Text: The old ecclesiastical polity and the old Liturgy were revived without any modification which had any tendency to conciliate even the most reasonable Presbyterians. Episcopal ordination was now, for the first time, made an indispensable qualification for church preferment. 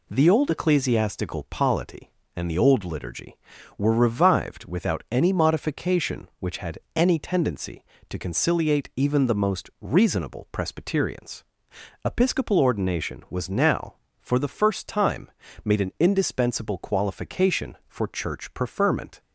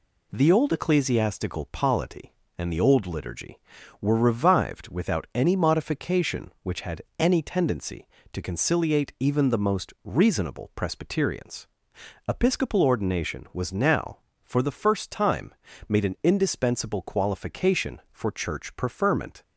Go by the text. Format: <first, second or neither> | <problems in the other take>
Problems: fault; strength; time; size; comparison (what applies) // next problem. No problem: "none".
neither | pauses between "had" and "any"; slight; the same in both